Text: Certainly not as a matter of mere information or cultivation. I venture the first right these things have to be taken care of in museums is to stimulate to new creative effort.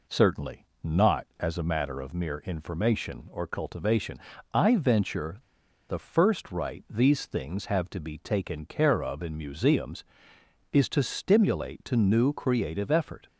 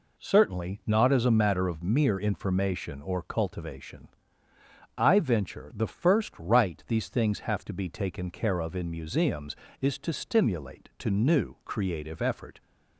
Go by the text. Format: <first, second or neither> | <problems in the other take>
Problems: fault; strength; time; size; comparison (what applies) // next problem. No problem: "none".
second | pauses between "Certainly" and "not"; slight; at 0.6 s; 0.18 s long // pauses between "venture" and "the"; noticeable; at 5.3 s; 0.52 s long